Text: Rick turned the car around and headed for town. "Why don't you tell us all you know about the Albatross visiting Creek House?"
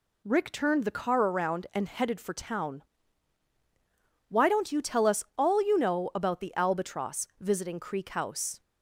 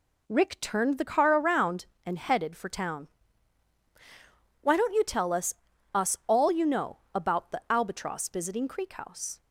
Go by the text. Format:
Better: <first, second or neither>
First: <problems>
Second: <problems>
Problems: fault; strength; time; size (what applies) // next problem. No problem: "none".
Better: first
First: none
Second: says "us" twice; at 5.9 s // pauses between "know" and "about"; slight; at 6.9 s; 0.16 s long